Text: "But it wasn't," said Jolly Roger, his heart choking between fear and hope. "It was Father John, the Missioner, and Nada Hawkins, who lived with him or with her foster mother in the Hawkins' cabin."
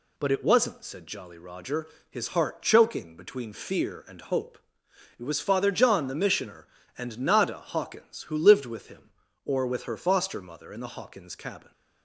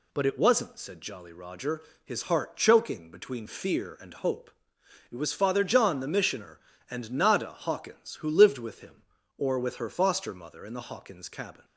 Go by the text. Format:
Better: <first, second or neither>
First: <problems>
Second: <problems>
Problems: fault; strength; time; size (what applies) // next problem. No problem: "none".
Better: neither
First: none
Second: none